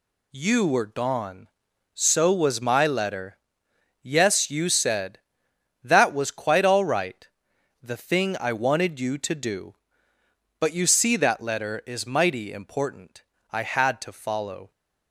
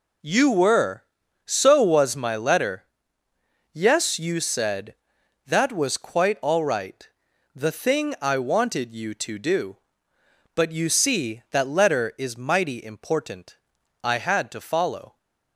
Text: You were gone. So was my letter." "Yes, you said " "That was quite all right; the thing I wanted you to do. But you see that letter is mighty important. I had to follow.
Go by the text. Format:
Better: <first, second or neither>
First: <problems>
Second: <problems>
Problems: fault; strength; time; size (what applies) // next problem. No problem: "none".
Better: first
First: none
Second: skips "gone"; at 1.2 s